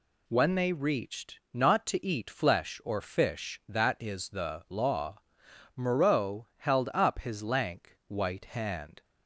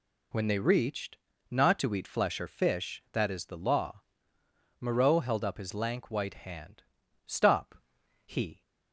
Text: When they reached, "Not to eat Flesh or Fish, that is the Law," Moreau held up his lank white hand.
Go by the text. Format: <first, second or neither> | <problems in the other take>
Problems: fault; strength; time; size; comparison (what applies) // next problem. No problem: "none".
first | goes on to say "Stop he"; from 7.2 s on; 1.3 s long